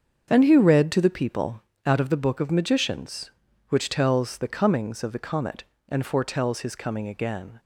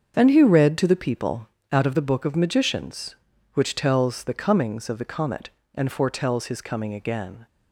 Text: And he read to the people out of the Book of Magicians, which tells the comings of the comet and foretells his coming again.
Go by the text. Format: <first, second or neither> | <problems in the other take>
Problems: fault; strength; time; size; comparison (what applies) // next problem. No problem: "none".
neither | starts louder than the rest; the same in both // pauses between "people" and "out"; slight; the same in both